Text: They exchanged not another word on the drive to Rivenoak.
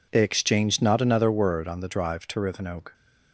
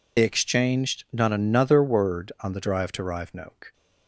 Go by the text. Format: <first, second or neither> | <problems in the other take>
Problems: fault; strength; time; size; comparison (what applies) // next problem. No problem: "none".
first | loses the start of "They"; at 0.1 s; 40 ms